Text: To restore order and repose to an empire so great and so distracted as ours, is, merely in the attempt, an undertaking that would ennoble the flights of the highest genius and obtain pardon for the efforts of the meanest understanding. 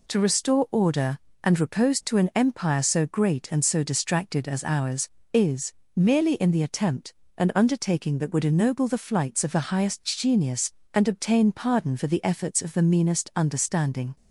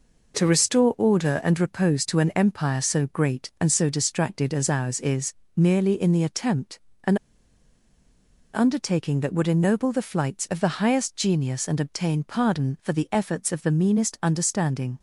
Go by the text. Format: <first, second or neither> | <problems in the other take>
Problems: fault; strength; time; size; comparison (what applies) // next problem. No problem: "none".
first | pauses between "an" and "undertaking"; strong; at 7.1 s; 1.3 s long